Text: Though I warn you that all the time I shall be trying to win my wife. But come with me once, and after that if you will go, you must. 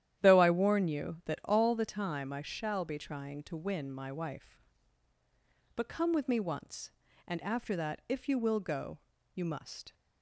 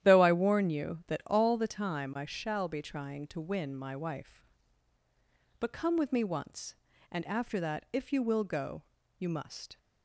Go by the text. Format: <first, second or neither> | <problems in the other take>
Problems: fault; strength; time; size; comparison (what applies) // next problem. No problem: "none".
neither | starts louder than the rest; strong; the same in both